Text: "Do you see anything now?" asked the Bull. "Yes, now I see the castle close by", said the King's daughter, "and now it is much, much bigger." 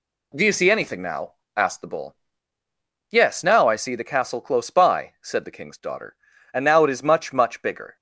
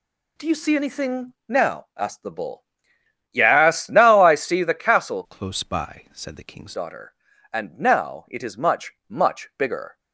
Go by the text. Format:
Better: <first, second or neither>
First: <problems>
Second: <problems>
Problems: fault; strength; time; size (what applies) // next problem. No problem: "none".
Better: first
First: none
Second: changes voice from "close" to "King's"; from 5.2 to 6.7 s; 1.5 s long